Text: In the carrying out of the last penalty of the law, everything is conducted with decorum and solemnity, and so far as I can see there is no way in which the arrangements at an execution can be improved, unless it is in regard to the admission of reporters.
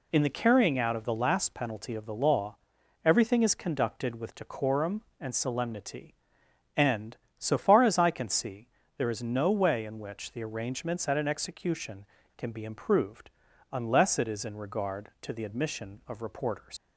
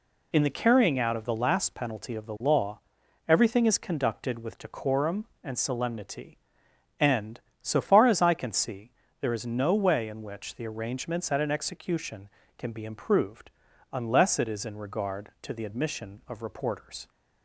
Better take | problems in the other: second | pauses between "see" and "there"; slight; at 8.6 s; 0.28 s long; slight in the second // leaves "reporters" unfinished; at 16.7 s; 110 ms

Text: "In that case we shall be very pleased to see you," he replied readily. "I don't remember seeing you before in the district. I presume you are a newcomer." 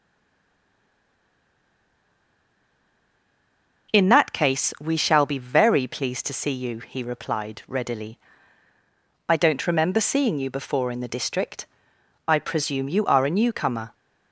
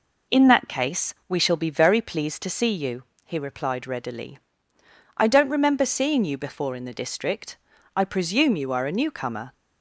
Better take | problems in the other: second | stays silent before the first word; strong; until 3.8 s; 3.8 s long

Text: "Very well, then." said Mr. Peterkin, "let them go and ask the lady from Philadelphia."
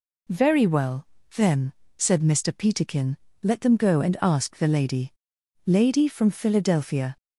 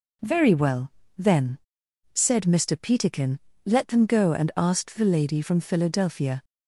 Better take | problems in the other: second | says "lady" twice; at 5.6 s

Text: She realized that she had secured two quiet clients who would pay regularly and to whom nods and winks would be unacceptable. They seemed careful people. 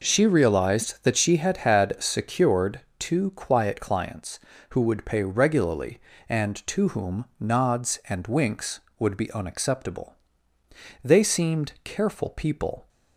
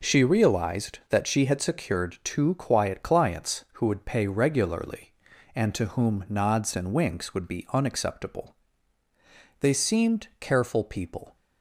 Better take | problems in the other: second | says "had" twice; at 1.5 s // pauses between "secured" and "two"; slight; at 2.8 s; 0.18 s long

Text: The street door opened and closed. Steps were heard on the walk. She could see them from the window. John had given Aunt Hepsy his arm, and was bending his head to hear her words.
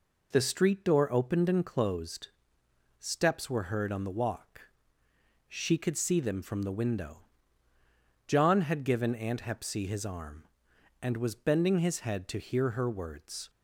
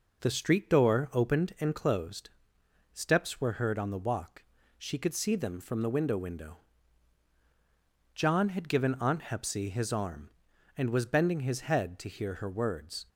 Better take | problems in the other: first | says "window" twice; at 6.1 s

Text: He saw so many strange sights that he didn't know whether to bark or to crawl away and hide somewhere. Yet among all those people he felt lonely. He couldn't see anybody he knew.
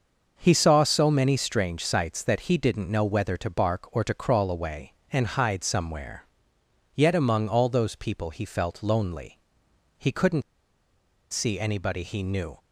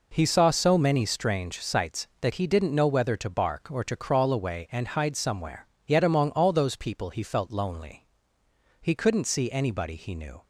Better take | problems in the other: second | starts louder than the rest; until 1.3 s; 6 dB // pauses between "couldn't" and "see"; noticeable; at 10.4 s; 0.89 s long

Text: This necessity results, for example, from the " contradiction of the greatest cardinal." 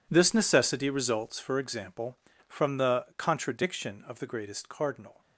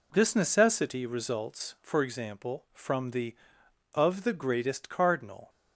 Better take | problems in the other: first | skips "contradiction"; at 3.9 s

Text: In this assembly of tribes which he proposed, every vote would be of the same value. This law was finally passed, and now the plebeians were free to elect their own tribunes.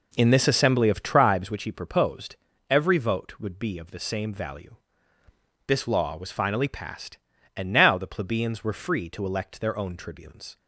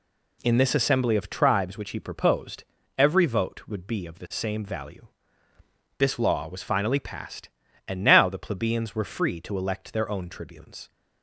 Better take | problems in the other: second | starts louder than the rest; noticeable; until 1.6 s; 4.5 dB

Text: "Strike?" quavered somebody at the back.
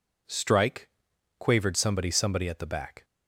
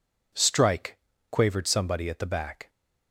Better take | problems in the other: second | says "somebody" twice; at 2.1 s

